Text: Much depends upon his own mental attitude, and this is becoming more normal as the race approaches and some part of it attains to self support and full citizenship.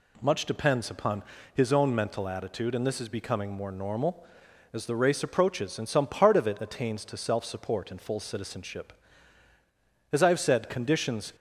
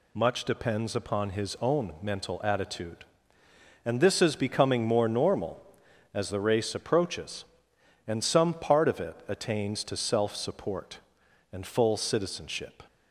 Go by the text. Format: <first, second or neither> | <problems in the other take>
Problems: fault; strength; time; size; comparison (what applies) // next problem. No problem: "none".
second | pauses between "upon" and "his"; slight; at 1.2 s; 0.32 s long // goes on to say "As I have said conditions"; noticeable; from 10.1 s on; 1.2 s long